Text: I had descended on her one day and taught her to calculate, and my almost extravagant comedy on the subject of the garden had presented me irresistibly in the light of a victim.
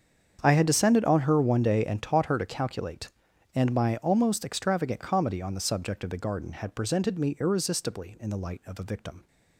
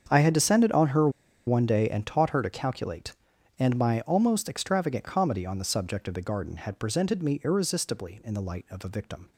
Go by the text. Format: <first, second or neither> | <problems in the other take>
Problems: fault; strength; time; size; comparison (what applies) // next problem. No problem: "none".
first | starts louder than the rest; strong; until 1.0 s; 7.5 dB; strong in the first // pauses between "her" and "one"; at 1.0 s; 0.37 s long